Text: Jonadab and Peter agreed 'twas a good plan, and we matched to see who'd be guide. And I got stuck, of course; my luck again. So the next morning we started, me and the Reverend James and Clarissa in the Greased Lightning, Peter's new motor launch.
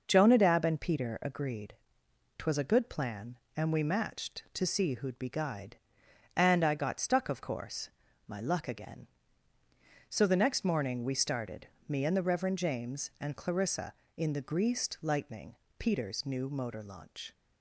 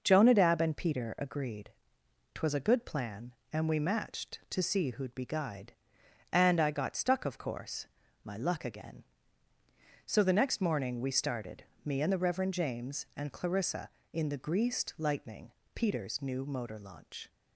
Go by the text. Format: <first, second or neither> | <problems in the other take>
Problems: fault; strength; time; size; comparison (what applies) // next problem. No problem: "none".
neither | pauses between "agreed" and "twas"; noticeable; the same in both